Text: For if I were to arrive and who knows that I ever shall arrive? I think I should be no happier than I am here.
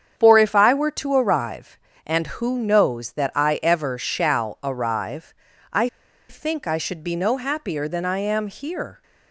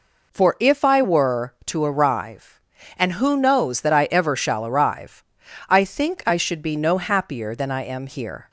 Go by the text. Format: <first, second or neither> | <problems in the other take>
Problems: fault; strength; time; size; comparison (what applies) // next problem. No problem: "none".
second | starts louder than the rest; strong; until 1.2 s; 8 dB // pauses between "I" and "think"; at 5.8 s; 0.41 s long